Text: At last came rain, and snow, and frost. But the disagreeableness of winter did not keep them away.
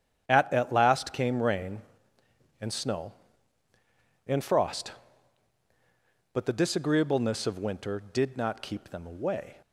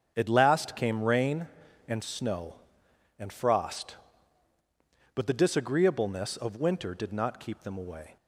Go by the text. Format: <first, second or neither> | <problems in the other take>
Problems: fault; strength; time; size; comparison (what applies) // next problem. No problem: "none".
second | starts louder than the rest; strong; until 1.2 s; 8.5 dB; strong in the second // says "At" twice; at 0.5 s